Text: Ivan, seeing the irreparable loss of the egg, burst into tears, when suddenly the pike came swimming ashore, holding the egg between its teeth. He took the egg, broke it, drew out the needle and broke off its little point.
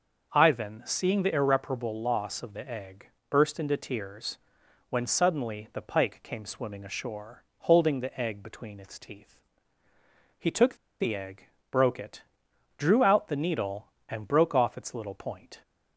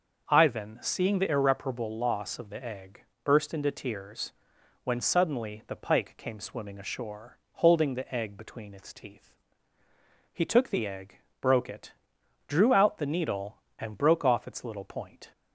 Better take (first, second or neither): second